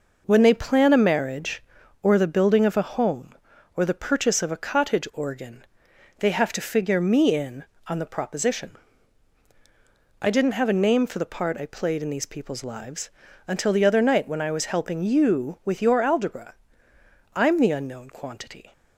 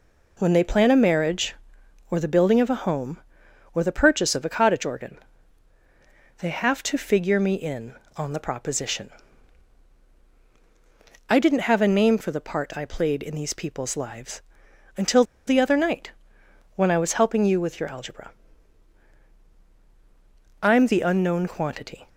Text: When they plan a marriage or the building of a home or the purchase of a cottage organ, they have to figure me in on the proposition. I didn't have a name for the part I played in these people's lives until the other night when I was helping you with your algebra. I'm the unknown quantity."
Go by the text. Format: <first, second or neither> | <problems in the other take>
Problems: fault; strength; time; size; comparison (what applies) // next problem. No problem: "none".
first | pauses between "lives" and "until"; noticeable; at 14.4 s; 0.52 s long; also in the first // pauses between "until" and "the"; slight; at 15.2 s; 0.24 s long // pauses between "night" and "when"; noticeable; at 16.1 s; 0.64 s long